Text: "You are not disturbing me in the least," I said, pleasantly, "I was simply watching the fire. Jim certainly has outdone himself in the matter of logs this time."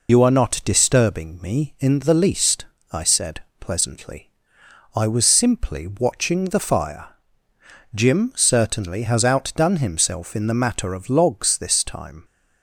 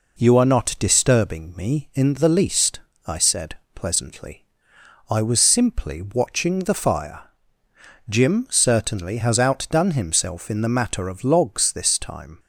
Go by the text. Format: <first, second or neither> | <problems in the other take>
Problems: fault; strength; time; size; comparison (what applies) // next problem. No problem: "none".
second | loses the start of "You"; at 0.0 s; 80 ms